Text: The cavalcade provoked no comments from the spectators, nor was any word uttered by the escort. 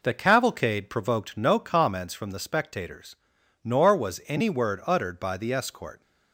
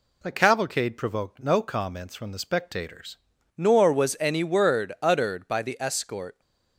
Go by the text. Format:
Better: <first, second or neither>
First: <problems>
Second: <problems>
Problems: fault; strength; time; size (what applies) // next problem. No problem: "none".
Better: first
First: none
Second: changes voice at "nor"; from 3.5 s on; 2.8 s long